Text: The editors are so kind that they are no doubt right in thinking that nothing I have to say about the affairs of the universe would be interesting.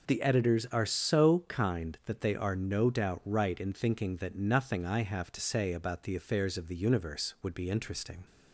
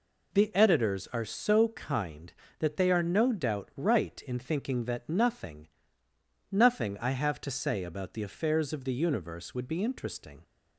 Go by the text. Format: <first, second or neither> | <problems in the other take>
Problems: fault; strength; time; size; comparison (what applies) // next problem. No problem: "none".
first | says "nothing" twice; at 6.5 s